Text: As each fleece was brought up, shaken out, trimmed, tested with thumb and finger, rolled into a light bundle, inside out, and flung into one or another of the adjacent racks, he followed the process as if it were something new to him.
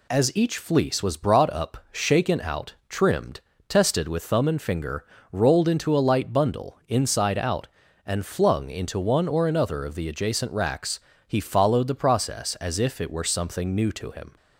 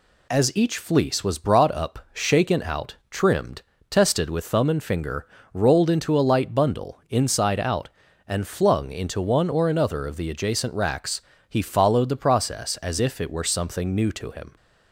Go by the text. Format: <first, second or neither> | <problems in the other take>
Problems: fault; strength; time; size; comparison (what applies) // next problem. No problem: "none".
neither | none